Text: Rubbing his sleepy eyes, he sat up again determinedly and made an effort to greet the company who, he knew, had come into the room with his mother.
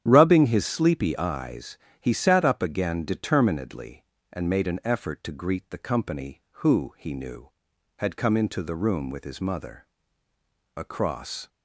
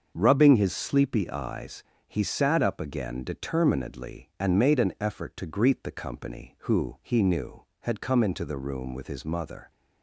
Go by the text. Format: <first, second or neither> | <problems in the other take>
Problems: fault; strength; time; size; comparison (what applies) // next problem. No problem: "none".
second | starts louder than the rest; strong; until 1.0 s; 9.5 dB; also in the second // goes on to say "Across"; noticeable; from 10.7 s on; 0.72 s long